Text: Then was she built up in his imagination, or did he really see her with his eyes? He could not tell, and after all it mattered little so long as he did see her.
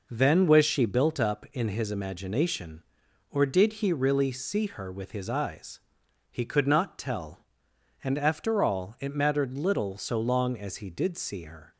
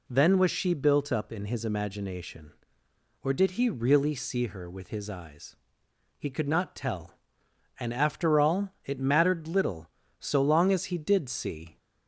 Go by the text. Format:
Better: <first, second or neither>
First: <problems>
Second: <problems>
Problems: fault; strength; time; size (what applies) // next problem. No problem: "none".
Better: first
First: none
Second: stops before "her"; at 11.7 s